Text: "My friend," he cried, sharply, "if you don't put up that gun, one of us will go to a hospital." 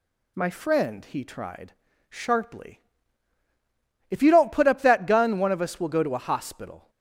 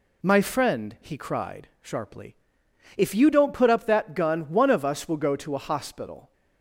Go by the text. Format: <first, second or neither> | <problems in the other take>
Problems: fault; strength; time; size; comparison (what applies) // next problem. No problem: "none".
second | says "tried" for "cried"; at 1.2 s